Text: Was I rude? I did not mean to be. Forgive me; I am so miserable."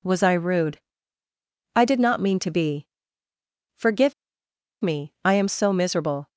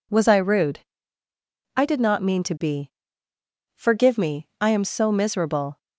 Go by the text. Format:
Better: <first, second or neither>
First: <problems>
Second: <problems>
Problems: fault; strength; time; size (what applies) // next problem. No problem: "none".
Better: second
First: pauses between "Forgive" and "me"; noticeable; at 4.1 s; 0.70 s long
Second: none